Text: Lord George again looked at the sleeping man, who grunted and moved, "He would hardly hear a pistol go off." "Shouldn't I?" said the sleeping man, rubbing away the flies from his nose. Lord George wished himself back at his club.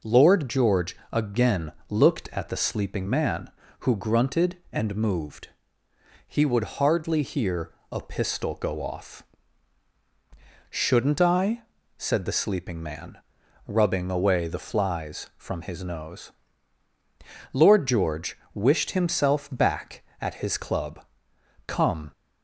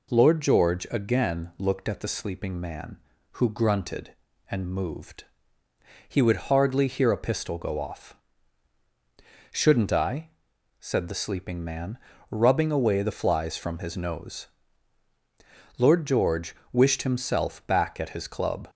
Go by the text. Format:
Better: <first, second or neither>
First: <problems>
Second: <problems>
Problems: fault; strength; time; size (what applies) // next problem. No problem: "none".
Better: second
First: pauses between "George" and "again"; slight; at 0.9 s; 0.16 s long // pauses between "again" and "looked"; slight; at 1.7 s; 0.18 s long // pauses between "hear" and "a"; slight; at 7.7 s; 0.18 s long // pauses between "George" and "wished"; slight; at 18.3 s; 0.18 s long // goes on to say "Come"; slight; from 21.6 s on; 0.44 s long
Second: pauses between "George" and "wished"; slight; at 16.5 s; 0.16 s long